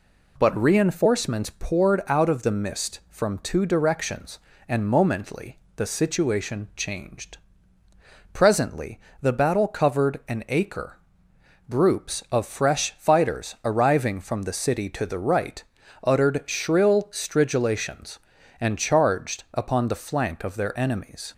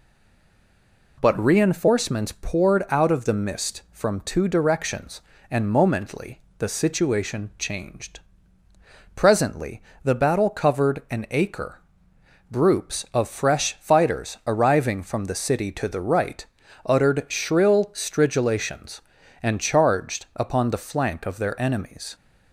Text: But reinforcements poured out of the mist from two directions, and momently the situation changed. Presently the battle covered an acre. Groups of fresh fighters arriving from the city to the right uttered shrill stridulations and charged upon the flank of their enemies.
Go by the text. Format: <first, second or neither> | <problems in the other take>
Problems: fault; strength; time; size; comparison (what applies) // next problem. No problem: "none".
first | stays silent before the first word; until 1.1 s; 1.1 s long // pauses between "momently" and "the"; slight; at 6.4 s; 0.18 s long; slight in the first // pauses between "Presently" and "the"; slight; at 9.8 s; 0.22 s long; slight in the first // pauses between "right" and "uttered"; at 16.4 s; 0.40 s long; also in the first